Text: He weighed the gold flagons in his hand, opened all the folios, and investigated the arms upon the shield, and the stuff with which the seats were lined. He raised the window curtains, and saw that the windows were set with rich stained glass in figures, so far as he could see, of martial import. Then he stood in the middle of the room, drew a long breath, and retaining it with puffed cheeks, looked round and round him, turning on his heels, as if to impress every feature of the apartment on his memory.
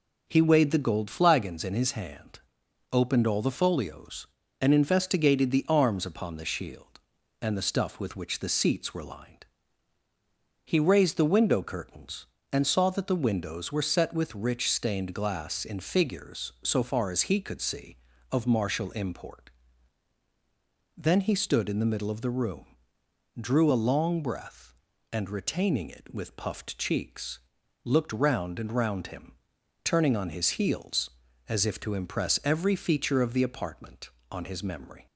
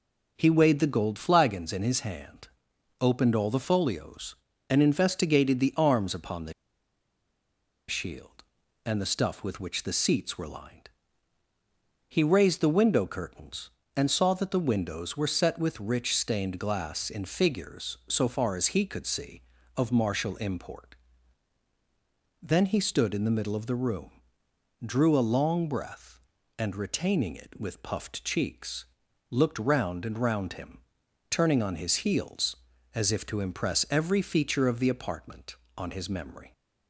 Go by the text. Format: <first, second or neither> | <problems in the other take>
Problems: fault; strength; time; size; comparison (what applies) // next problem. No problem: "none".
first | pauses between "the" and "shield"; strong; at 6.5 s; 1.3 s long